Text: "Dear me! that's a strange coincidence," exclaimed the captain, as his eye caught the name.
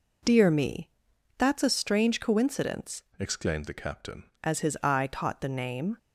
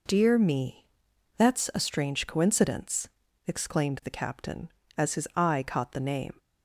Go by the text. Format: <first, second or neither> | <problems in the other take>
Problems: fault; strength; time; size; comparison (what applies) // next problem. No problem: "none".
second | changes voice from "exclaimed" to "captain"; from 3.1 to 4.2 s; 1.1 s long